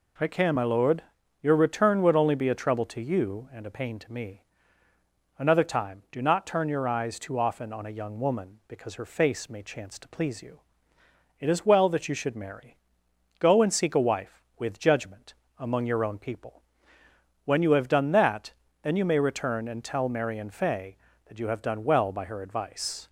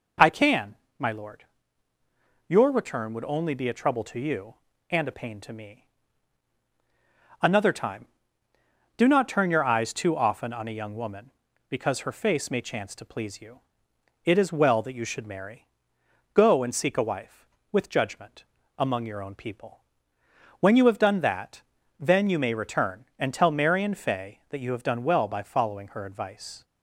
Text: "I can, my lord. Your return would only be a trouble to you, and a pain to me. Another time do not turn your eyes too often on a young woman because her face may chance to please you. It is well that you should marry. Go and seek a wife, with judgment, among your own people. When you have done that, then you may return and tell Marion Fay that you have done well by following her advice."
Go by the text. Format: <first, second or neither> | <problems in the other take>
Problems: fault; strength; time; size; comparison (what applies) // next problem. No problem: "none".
second | skips "following"; at 22.2 s